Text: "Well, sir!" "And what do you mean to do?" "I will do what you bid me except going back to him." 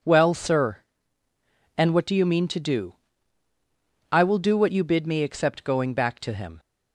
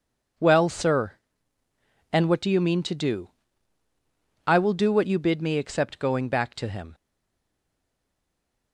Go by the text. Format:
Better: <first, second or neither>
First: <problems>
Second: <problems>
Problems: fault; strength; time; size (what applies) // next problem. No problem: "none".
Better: first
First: none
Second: stays silent after the last word; noticeable; from 6.9 s on; 1.8 s long